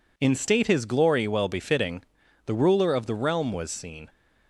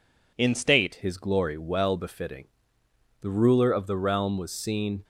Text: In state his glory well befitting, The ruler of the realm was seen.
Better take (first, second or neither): first